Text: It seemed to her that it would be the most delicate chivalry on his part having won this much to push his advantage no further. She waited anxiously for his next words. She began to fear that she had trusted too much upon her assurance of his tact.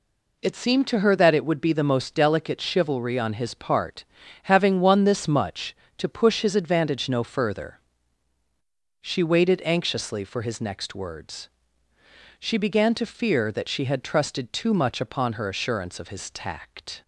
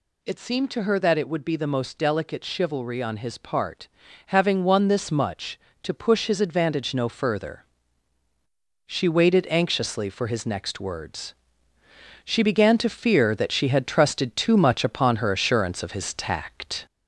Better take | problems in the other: first | gets louder; slight; throughout; 2.5 dB // pauses between "part" and "having"; at 3.8 s; 0.40 s long; also in the first

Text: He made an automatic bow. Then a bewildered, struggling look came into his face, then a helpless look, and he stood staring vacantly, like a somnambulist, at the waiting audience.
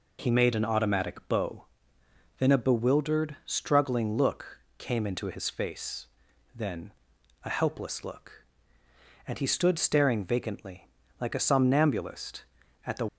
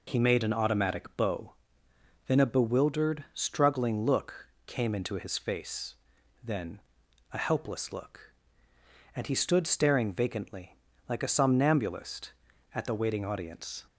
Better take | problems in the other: second | pauses between "look" and "came"; slight; at 4.5 s; 0.18 s long; slight in the second // pauses between "then" and "a"; noticeable; at 6.9 s; 0.50 s long; noticeable in the second // stops before "waiting audience"; at 13.0 s

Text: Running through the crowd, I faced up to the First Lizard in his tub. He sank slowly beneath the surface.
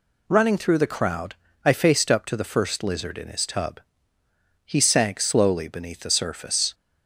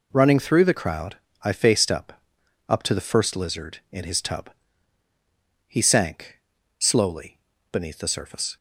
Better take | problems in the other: first | says "up" twice; at 2.6 s // pauses between "sank" and "slowly"; at 6.3 s; 0.40 s long // pauses between "slowly" and "beneath"; slight; at 7.3 s; 0.34 s long

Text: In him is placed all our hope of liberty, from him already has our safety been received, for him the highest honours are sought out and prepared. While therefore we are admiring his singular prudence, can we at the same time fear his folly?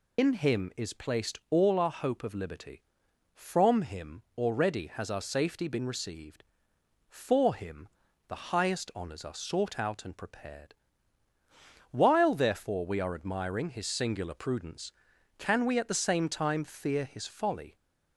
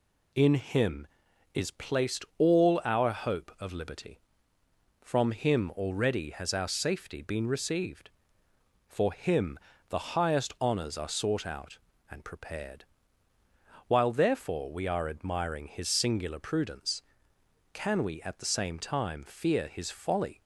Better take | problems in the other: second | loses the start of "In"; at 0.1 s; 90 ms // pauses between "him" and "already"; slight; at 4.2 s; 0.16 s long // pauses between "him" and "the"; at 7.8 s; 0.40 s long; slight in the second

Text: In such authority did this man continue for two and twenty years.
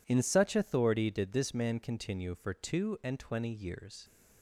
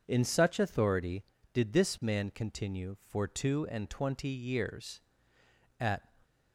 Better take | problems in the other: first | goes on to say "At"; slight; from 5.7 s on; 0.30 s long

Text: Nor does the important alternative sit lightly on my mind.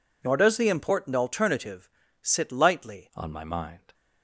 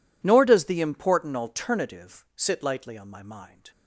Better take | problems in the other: second | pauses between "alternative" and "sit"; slight; at 1.8 s; 0.34 s long // changes voice at "on"; from 3.1 s on; 0.8 s long

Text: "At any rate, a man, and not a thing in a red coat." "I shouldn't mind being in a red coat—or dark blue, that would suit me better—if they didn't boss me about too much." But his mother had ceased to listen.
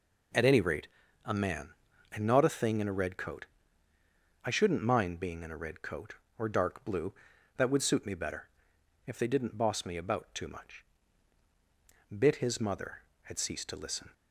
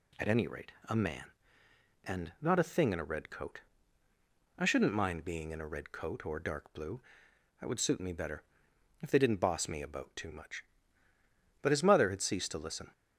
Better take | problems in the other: second | says "Bit" for "But"; at 12.1 s

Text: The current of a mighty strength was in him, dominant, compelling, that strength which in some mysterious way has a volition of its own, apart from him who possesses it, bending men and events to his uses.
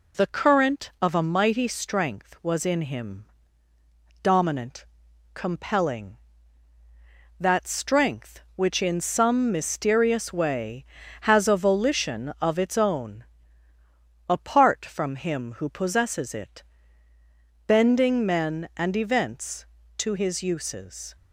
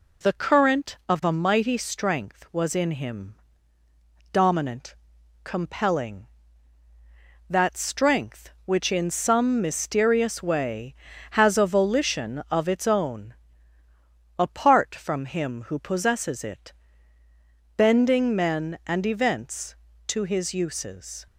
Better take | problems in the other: neither | none

